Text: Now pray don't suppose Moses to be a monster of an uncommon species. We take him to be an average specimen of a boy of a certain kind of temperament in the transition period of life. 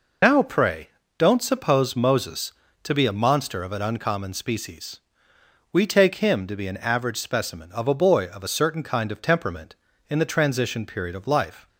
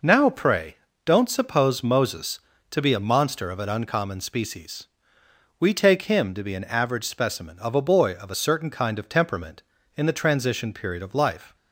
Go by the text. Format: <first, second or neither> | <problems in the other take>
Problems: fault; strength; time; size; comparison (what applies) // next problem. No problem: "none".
second | loses the start of "Now"; at 0.2 s; 70 ms // pauses between "pray" and "don't"; slight; at 0.8 s; 0.28 s long; slight in the second